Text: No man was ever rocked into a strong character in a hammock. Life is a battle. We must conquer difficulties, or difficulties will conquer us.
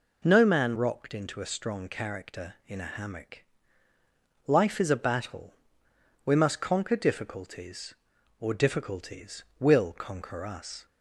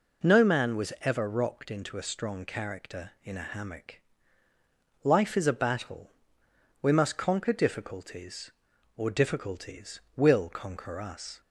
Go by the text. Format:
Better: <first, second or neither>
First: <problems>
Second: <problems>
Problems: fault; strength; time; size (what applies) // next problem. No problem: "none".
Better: second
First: skips "was ever"; at 0.7 s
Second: none